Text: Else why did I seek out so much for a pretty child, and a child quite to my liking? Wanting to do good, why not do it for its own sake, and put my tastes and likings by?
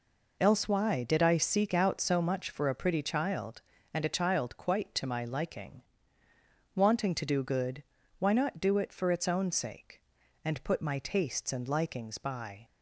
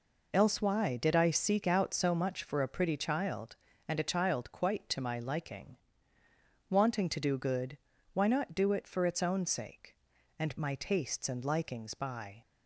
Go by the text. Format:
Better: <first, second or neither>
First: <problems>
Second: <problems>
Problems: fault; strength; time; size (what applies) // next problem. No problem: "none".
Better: first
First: none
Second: skips "put"; at 10.5 s